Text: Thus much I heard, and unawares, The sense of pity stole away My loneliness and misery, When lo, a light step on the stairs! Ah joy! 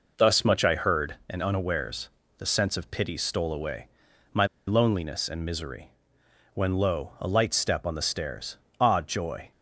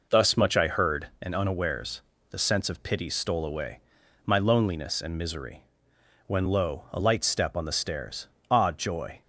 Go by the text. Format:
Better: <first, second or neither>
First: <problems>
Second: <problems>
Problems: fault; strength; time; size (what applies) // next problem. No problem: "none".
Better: second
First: pauses between "away" and "My"; at 3.8 s; 0.44 s long // pauses between "My" and "loneliness"; slight; at 4.4 s; 0.22 s long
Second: pauses between "away" and "My"; at 3.7 s; 0.44 s long